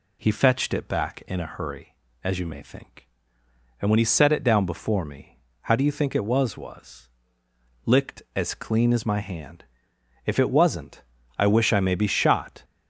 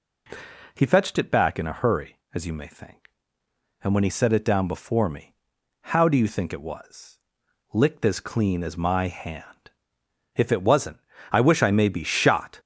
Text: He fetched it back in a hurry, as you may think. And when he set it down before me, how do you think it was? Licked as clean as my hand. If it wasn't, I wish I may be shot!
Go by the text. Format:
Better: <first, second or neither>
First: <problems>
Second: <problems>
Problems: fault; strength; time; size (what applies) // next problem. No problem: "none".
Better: second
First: says "was" twice; at 6.5 s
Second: none